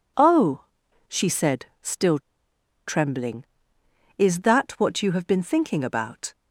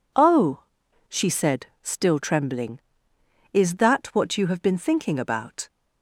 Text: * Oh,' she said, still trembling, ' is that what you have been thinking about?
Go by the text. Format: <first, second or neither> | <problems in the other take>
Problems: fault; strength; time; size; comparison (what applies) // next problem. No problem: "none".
second | pauses between "still" and "trembling"; noticeable; at 2.1 s; 0.67 s long